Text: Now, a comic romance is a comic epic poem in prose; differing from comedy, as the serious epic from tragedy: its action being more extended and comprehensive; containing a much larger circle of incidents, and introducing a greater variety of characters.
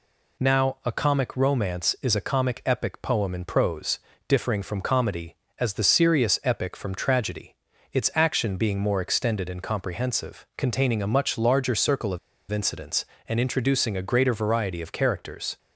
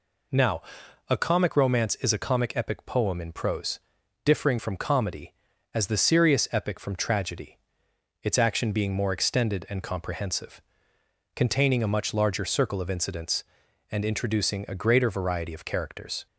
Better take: second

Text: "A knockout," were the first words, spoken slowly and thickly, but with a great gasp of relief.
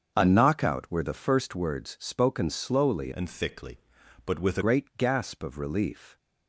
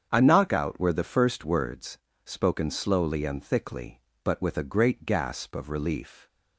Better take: second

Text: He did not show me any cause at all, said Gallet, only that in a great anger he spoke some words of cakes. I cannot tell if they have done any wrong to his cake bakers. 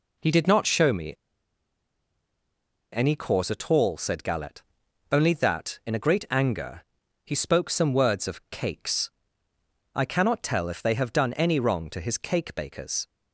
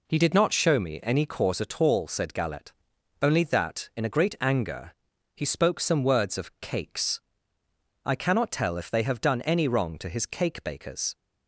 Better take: second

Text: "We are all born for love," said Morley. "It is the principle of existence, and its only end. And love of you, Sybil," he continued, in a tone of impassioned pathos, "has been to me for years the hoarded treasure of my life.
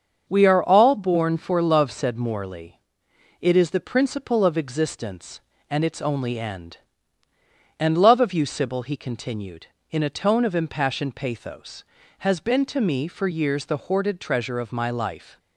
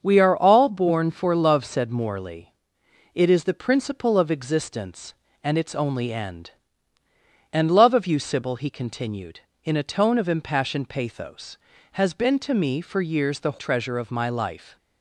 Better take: first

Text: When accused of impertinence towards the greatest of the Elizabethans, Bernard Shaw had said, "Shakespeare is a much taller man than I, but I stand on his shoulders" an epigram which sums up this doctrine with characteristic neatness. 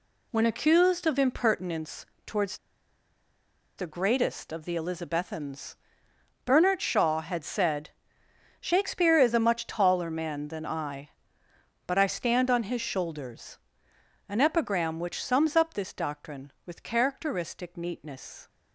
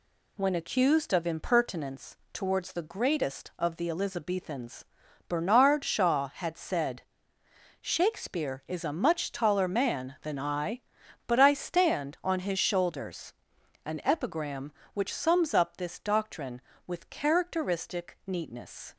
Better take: second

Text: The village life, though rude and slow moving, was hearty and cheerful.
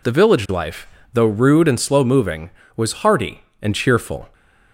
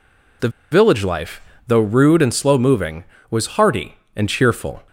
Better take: first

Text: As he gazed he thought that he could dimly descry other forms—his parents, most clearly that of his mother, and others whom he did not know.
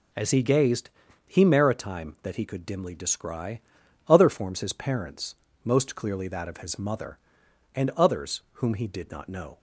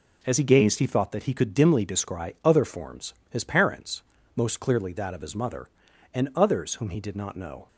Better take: second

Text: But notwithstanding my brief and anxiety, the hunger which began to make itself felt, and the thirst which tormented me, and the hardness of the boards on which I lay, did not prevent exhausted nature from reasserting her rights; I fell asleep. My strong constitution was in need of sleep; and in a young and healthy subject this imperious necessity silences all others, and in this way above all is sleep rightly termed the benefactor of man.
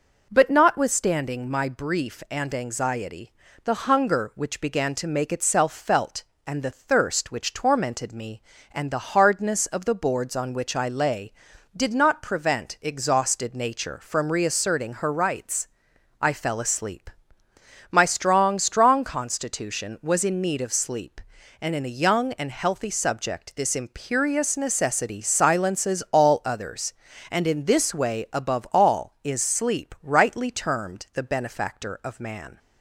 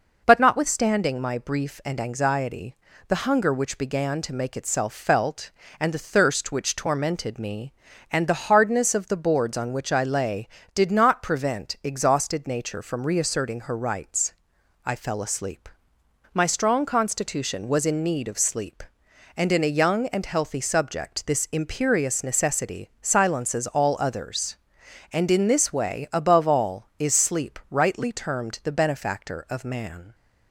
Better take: second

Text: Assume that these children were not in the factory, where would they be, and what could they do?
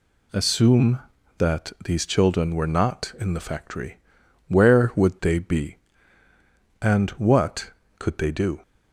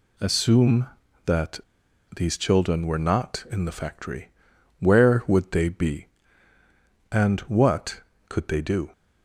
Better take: first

